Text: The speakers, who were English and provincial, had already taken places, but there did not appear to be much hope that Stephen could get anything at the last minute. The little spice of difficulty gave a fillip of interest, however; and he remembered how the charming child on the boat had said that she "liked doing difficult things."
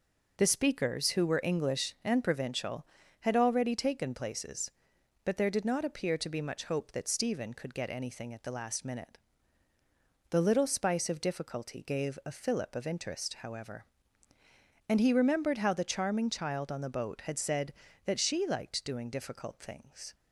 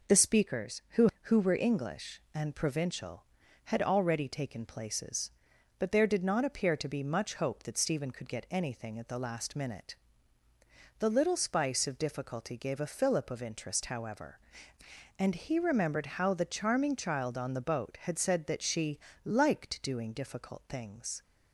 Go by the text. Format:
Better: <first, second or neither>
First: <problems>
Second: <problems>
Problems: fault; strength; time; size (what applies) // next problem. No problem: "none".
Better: first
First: none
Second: says "who" twice; at 1.2 s // pauses between "she" and "liked"; slight; at 18.9 s; 0.26 s long